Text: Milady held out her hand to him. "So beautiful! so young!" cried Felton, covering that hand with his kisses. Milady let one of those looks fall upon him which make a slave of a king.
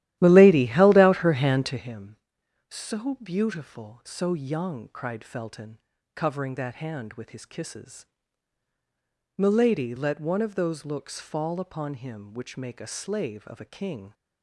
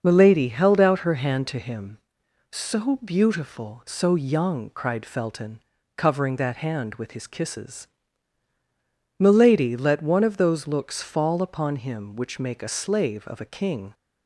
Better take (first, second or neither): second